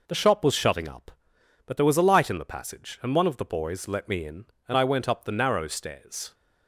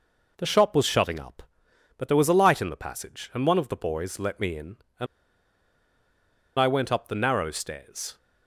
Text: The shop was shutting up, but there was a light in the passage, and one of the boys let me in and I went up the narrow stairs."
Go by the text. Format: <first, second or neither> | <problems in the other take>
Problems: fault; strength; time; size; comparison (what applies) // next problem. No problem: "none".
first | pauses between "and" and "I"; strong; at 5.0 s; 1.5 s long